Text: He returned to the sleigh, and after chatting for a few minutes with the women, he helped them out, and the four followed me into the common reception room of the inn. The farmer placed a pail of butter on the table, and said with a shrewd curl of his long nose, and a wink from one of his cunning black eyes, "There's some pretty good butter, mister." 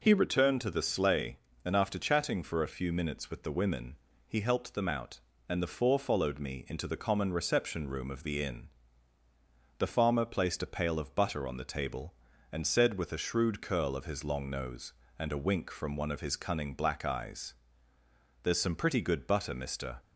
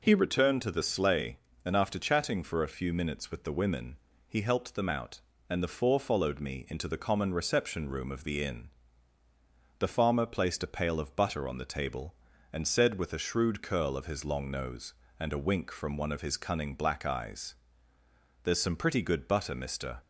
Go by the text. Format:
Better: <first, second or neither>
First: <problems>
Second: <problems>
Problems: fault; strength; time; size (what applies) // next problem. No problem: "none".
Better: neither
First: none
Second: none